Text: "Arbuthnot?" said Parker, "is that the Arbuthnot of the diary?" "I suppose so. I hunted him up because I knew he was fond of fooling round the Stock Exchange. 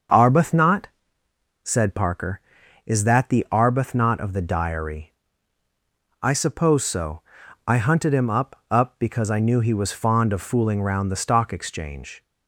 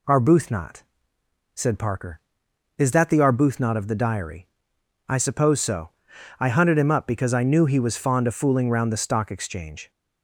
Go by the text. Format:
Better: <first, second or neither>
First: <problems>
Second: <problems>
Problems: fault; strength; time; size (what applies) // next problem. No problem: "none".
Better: second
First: starts louder than the rest; until 1.8 s; 6.5 dB // says "up" twice; at 8.7 s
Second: none